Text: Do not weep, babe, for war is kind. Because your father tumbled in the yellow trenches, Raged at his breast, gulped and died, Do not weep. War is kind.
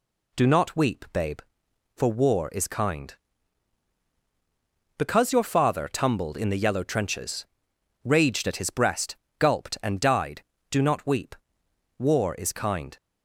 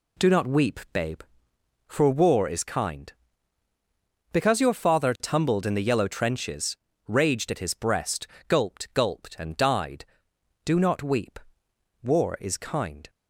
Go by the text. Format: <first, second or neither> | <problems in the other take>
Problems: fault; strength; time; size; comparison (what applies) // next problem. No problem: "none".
first | says "gulped" twice; at 8.9 s